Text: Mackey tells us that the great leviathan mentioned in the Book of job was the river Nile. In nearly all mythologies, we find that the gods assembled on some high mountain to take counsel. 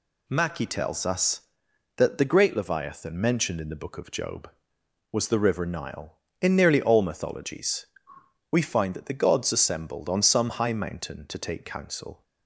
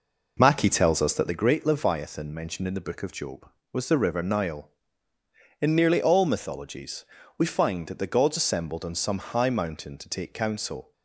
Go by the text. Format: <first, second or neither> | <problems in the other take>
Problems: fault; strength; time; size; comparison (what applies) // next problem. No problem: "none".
first | starts louder than the rest; noticeable; until 1.4 s; 4.5 dB